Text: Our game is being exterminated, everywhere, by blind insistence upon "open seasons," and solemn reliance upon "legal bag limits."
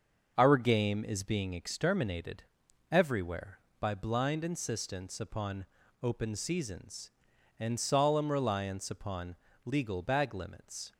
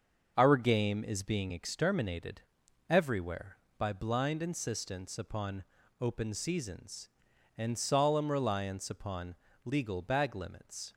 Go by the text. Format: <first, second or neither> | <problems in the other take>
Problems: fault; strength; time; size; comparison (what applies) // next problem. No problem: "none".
neither | pauses between "upon" and "open"; slight; the same in both // pauses between "upon" and "legal"; slight; the same in both